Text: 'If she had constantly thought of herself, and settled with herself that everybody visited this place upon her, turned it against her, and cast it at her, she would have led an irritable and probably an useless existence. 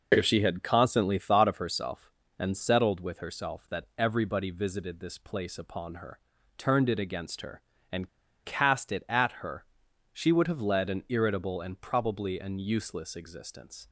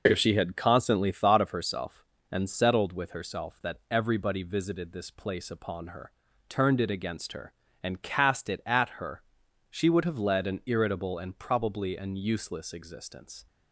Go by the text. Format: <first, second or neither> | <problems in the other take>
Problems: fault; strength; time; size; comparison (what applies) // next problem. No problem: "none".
second | pauses between "and" and "cast"; slight; at 8.0 s; 0.35 s long